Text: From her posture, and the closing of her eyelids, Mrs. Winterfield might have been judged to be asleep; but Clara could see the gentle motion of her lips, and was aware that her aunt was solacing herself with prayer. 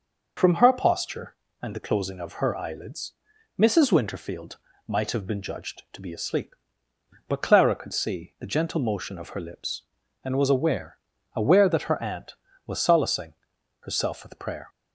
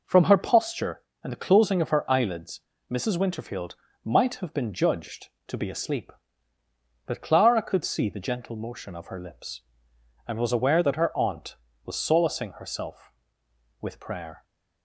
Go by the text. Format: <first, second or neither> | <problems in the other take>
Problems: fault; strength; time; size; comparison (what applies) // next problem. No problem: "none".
second | pauses between "Winterfield" and "might"; slight; at 4.5 s; 0.28 s long; slight in the second // says "aware" twice; at 11.3 s // pauses between "solacing" and "herself"; noticeable; at 13.3 s; 0.48 s long